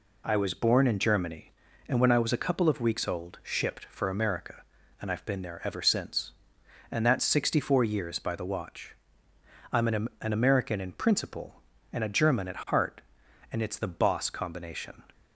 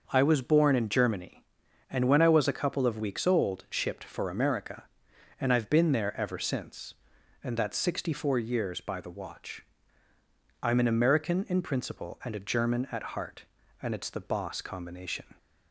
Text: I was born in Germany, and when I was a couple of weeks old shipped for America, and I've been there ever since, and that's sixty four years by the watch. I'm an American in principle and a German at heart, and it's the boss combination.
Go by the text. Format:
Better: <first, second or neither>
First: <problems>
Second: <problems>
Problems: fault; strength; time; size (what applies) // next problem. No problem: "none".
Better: second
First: says "an" twice; at 10.2 s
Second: none